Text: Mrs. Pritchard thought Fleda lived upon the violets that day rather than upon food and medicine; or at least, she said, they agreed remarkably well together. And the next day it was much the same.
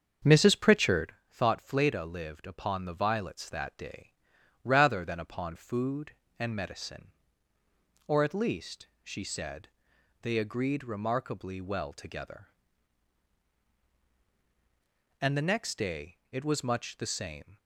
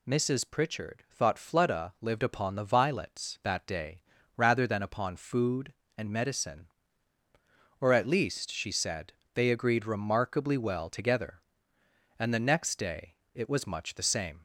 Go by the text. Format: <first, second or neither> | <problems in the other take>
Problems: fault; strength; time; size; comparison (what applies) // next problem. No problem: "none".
second | starts louder than the rest; strong; until 1.2 s; 7 dB // pauses between "Pritchard" and "thought"; slight; at 1.1 s; 0.18 s long // pauses between "day" and "rather"; noticeable; at 4.1 s; 0.52 s long; slight in the second // pauses between "day" and "it"; slight; at 16.1 s; 0.16 s long; slight in the second